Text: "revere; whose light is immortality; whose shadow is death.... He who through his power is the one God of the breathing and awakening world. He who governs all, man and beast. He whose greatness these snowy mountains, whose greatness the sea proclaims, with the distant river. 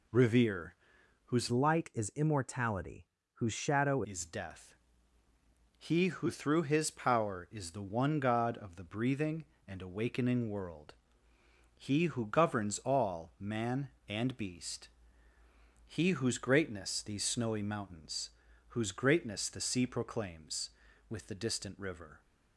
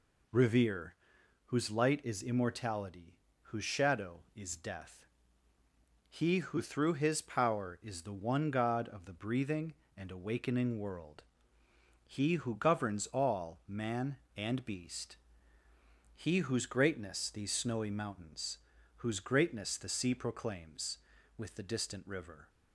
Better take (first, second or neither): second